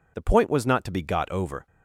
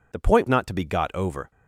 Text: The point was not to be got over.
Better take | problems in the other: first | skips "was"; at 0.4 s

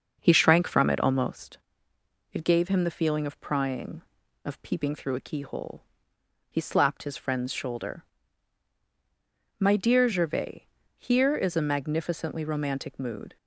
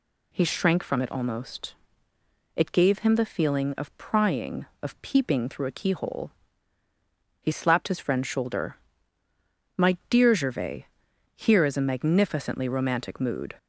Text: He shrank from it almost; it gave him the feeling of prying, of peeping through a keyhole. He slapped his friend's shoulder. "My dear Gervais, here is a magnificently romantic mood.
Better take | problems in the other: second | starts louder than the rest; until 1.6 s; 6.5 dB

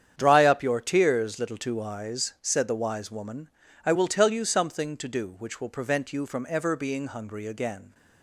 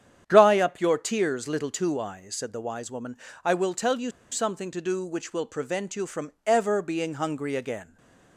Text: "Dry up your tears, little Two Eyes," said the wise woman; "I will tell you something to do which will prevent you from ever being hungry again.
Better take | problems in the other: first | starts louder than the rest; strong; until 1.2 s; 9.5 dB; strong in the first // pauses between "you" and "something"; slight; at 4.0 s; 0.23 s long // stays silent after the last word; slight; from 7.8 s on; 0.5 s long

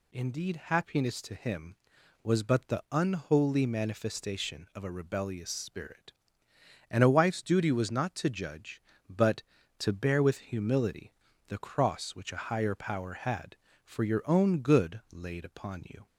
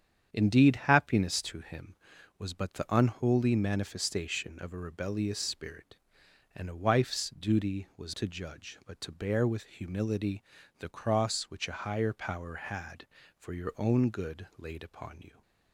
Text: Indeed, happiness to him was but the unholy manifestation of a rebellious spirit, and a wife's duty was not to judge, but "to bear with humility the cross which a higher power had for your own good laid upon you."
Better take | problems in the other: first | starts louder than the rest; strong; until 1.3 s; 8.5 dB // skips "not"; at 8.1 s // pauses between "humility" and "the"; slight; at 10.4 s; 0.34 s long; slight in the first

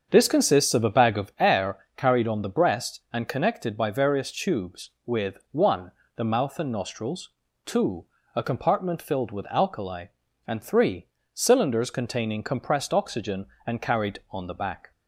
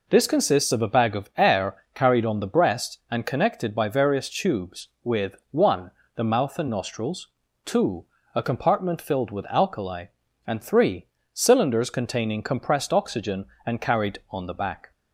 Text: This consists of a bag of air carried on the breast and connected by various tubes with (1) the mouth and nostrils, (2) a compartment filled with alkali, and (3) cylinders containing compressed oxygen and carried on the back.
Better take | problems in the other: second | starts louder than the rest; until 1.5 s; 7 dB // pauses between "air" and "carried"; slight; at 1.7 s; 0.20 s long; slight in the second

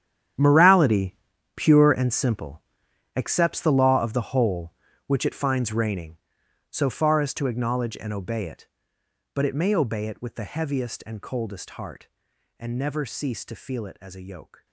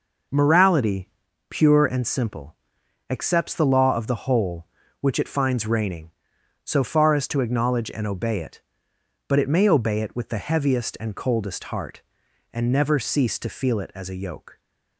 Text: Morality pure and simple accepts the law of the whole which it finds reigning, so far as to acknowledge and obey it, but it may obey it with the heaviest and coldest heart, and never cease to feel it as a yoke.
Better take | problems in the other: second | gets quieter; strong; throughout; 14.5 dB // pauses between "Morality" and "pure"; at 1.1 s; 0.38 s long; also in the second // pauses between "simple" and "accepts"; noticeable; at 2.5 s; 0.56 s long; noticeable in the second

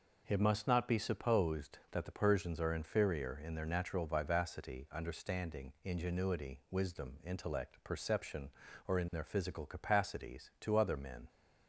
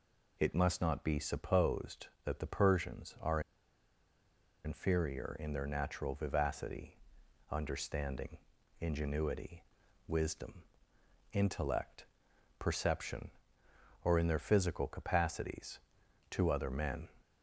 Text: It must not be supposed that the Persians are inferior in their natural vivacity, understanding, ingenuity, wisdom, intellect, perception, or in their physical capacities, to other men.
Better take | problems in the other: first | pauses between "are" and "inferior"; strong; at 3.3 s; 1.2 s long

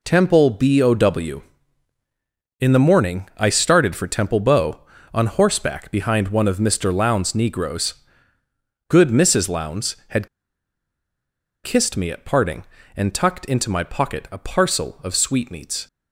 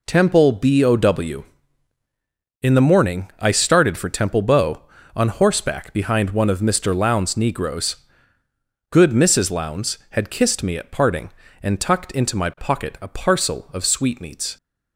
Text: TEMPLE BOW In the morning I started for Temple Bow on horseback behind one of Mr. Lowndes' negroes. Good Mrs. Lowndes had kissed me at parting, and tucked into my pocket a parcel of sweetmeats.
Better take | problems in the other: second | pauses between "had" and "kissed"; strong; at 10.2 s; 1.3 s long

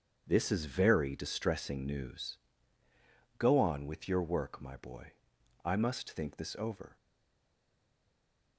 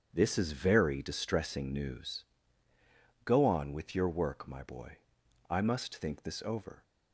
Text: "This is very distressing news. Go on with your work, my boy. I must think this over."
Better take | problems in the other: second | starts louder than the rest; strong; until 1.2 s; 7.5 dB; strong in the second // stays silent after the last word; noticeable; from 6.9 s on; 1.6 s long

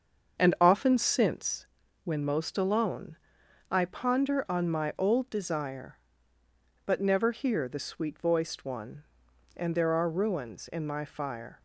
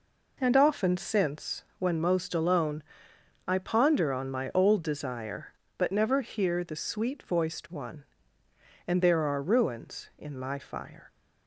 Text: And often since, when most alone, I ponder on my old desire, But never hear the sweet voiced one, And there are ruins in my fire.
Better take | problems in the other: second | starts louder than the rest; until 1.5 s; 7 dB

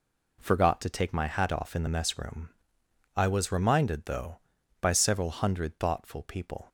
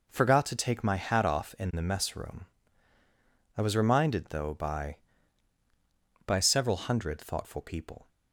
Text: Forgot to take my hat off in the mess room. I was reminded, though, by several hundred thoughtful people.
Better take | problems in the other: first | says "by" twice; at 6.2 s

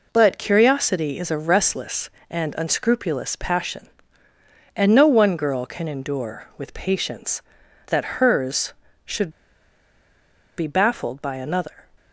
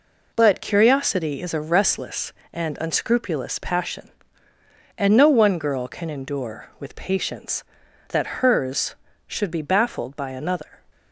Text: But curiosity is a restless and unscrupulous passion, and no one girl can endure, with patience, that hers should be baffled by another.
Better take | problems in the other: second | pauses between "should" and "be"; strong; at 9.2 s; 1.2 s long

